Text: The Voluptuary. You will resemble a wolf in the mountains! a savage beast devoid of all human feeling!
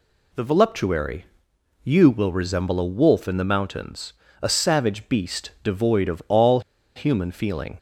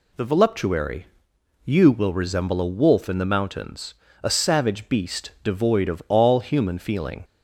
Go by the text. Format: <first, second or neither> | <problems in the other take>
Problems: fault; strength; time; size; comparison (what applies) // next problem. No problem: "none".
second | pauses between "all" and "human"; slight; at 6.5 s; 0.36 s long